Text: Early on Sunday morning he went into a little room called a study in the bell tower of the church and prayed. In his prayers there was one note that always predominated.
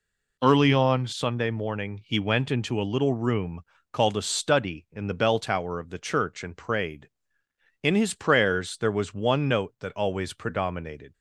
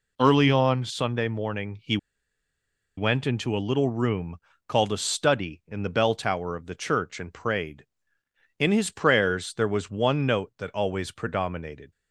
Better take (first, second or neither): first